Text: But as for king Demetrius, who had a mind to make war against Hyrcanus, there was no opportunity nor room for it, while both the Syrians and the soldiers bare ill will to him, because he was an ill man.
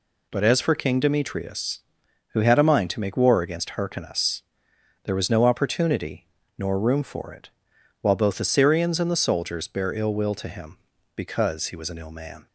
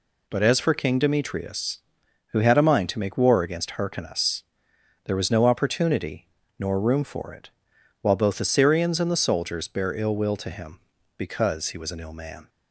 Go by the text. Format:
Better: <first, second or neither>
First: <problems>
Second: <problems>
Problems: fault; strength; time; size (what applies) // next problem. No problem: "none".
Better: neither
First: pauses between "opportunity" and "nor"; slight; at 6.2 s; 0.28 s long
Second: pauses between "opportunity" and "nor"; slight; at 6.2 s; 0.28 s long